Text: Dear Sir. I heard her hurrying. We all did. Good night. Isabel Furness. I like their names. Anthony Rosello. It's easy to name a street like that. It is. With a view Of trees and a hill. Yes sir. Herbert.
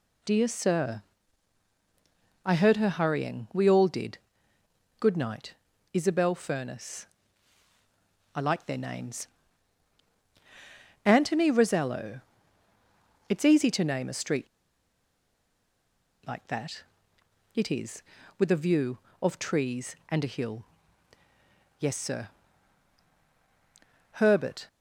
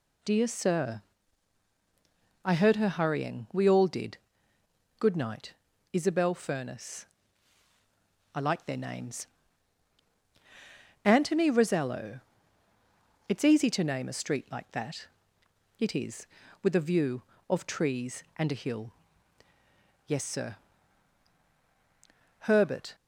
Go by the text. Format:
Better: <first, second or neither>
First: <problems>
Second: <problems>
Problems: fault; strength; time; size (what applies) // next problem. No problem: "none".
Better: second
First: pauses between "street" and "like"; strong; at 14.4 s; 1.8 s long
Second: none